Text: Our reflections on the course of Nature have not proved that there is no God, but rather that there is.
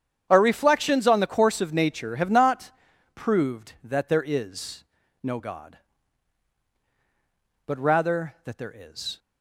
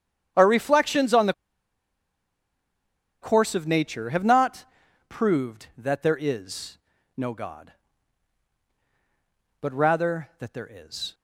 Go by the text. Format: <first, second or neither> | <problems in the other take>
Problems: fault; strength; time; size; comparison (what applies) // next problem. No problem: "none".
first | starts louder than the rest; strong; until 3.2 s; 8.5 dB; strong in the first // pauses between "the" and "course"; strong; at 1.3 s; 1.8 s long // pauses between "not" and "proved"; at 4.6 s; 0.44 s long; also in the first // pauses between "is" and "no"; at 6.7 s; 0.38 s long; also in the first